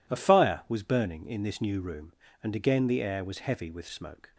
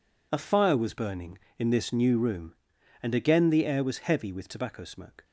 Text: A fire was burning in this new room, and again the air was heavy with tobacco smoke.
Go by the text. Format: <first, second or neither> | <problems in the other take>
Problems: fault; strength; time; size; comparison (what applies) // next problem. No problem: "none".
second | skips "tobacco"; at 3.8 s